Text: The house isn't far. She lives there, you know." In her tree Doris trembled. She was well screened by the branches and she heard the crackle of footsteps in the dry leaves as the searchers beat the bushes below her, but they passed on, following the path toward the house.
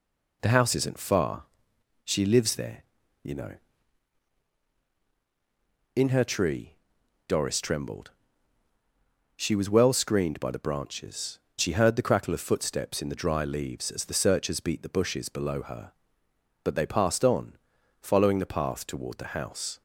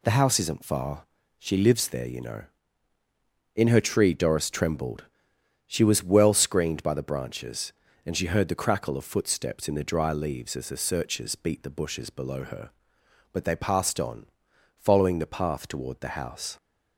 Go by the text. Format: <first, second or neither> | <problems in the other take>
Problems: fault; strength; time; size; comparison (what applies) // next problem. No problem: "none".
second | pauses between "tree" and "Doris"; noticeable; at 6.7 s; 0.52 s long // skips "and"; at 11.4 s